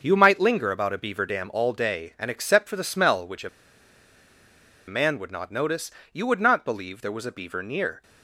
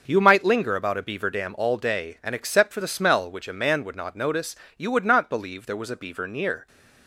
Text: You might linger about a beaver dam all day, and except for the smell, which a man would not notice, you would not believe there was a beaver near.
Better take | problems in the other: second | starts louder than the rest; until 1.0 s; 6.5 dB; also in the second // pauses between "a" and "man"; strong; at 3.4 s; 1.3 s long

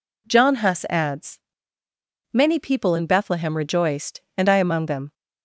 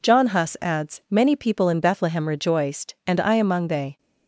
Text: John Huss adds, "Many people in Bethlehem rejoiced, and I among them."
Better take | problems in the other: first | says "they" for "them"; at 3.6 s

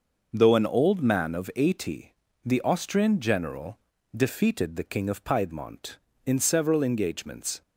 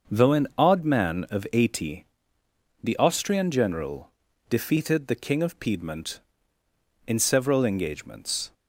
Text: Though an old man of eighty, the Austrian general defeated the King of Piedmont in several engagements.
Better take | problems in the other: first | starts louder than the rest; noticeable; until 1.1 s; 6 dB // says "odd" for "old"; at 0.5 s // pauses between "general" and "defeated"; at 4.1 s; 0.38 s long; slight in the first

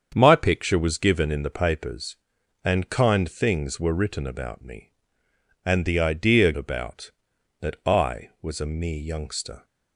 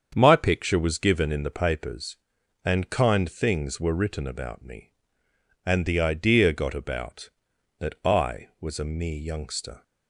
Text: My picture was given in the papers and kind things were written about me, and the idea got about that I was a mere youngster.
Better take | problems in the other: second | starts louder than the rest; strong; until 1.1 s; 7.5 dB; strong in the second // skips "got"; at 6.5 s

